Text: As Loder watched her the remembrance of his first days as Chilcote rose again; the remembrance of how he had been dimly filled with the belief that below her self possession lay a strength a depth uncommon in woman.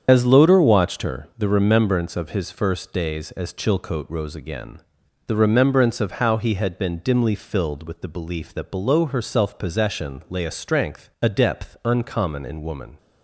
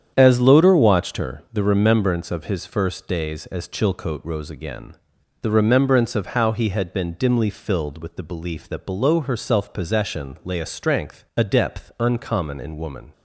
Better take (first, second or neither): second